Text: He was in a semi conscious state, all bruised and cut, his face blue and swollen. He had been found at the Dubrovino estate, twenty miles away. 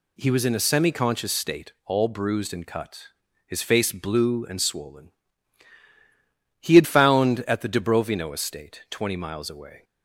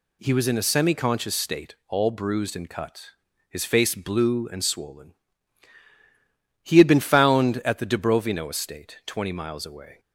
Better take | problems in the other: second | skips "been"; at 6.8 s

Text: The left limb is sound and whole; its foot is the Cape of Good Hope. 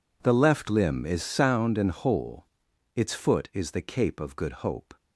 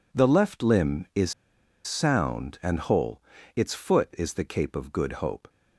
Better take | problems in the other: first | pauses between "is" and "sound"; noticeable; at 1.3 s; 0.53 s long

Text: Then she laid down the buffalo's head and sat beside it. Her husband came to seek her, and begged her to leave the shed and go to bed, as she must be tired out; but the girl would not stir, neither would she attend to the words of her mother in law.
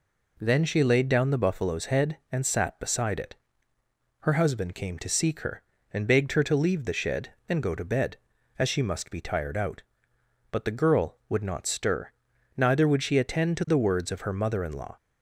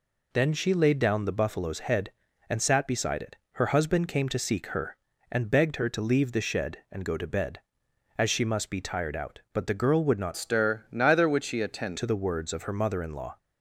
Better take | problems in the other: first | changes voice from "stir" to "attend"; from 10.3 to 11.9 s; 1.6 s long

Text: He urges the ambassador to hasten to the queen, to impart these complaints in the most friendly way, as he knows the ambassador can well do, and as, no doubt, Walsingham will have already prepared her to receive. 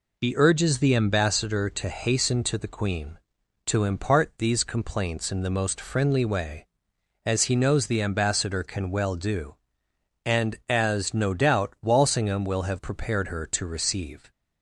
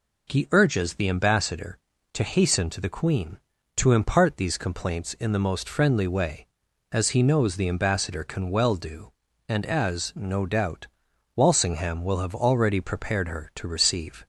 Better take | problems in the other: second | skips "already"; at 12.7 s

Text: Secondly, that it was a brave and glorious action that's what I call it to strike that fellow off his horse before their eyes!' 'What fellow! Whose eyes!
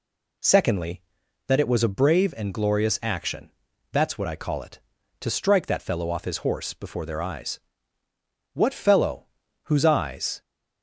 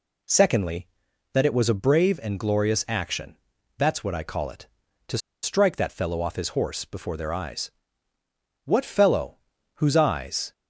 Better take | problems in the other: first | pauses between "action" and "that's"; at 3.3 s; 0.42 s long; also in the first // pauses between "to" and "strike"; slight; at 5.1 s; 0.25 s long

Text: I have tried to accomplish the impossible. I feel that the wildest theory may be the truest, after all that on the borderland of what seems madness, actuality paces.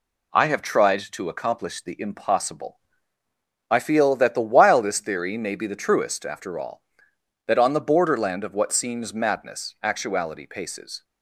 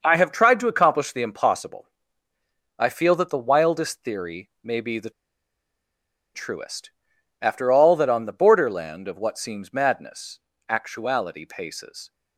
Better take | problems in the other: first | starts louder than the rest; noticeable; until 1.0 s; 6 dB // pauses between "the" and "truest"; at 5.1 s; 1.2 s long

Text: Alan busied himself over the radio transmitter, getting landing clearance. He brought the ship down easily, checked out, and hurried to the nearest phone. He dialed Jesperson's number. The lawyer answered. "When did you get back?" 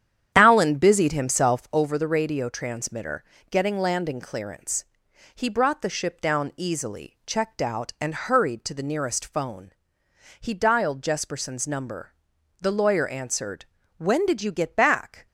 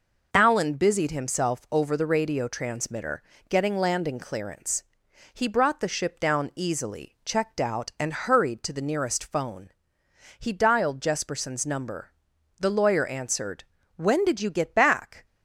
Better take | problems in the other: second | starts louder than the rest; strong; until 1.9 s; 9.5 dB

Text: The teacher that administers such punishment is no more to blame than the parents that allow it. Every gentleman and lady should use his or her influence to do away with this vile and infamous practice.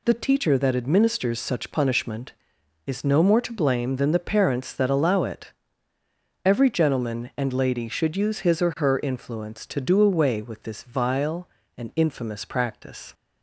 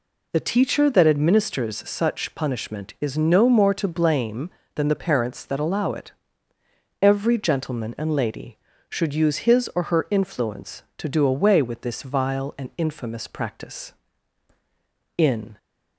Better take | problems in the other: first | goes on to say "In"; slight; from 15.1 s on; 0.40 s long

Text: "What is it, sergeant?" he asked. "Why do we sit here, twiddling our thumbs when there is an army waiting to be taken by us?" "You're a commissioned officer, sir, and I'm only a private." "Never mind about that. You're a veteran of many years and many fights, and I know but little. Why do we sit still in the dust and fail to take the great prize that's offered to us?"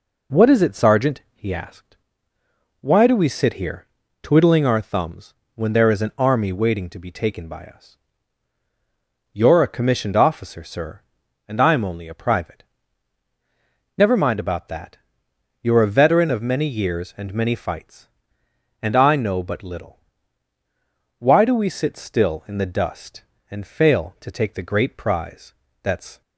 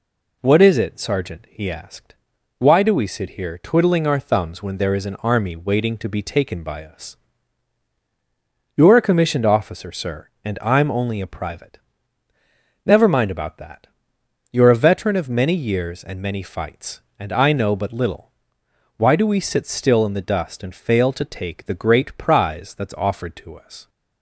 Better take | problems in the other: second | pauses between "thumbs" and "when"; slight; at 5.3 s; 0.22 s long // pauses between "prize" and "that's"; slight; at 25.5 s; 0.30 s long // stops before "offered to us"; at 26.2 s

